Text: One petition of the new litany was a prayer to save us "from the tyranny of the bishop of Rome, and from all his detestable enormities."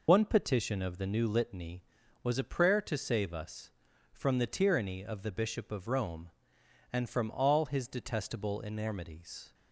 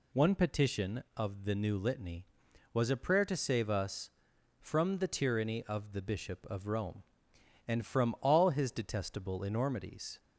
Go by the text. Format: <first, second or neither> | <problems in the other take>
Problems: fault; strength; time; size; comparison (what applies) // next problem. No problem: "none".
second | loses the start of "One"; at 0.0 s; 50 ms